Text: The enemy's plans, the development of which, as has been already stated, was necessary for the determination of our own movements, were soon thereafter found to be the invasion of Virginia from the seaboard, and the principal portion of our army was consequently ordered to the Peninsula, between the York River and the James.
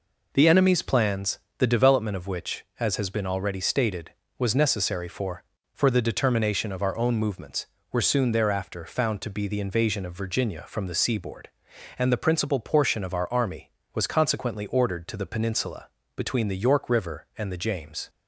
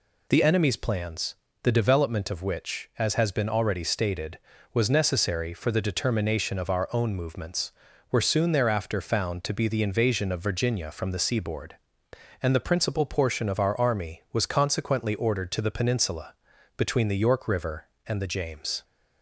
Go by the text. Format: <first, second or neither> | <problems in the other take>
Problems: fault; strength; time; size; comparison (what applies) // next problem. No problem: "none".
second | says "for" twice; at 5.7 s